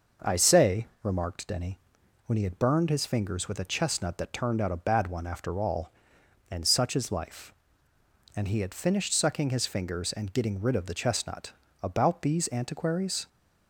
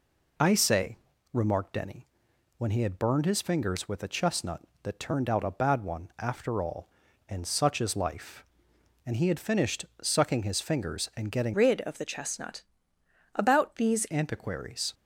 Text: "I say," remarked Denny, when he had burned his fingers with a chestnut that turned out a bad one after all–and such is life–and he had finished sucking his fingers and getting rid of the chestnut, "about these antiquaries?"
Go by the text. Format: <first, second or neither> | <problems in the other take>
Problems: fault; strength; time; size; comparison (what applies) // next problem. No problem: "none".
first | pauses between "finished" and "sucking"; slight; at 9.8 s; 0.18 s long // changes voice from "rid" to "these"; from 11.5 to 14.0 s; 2.5 s long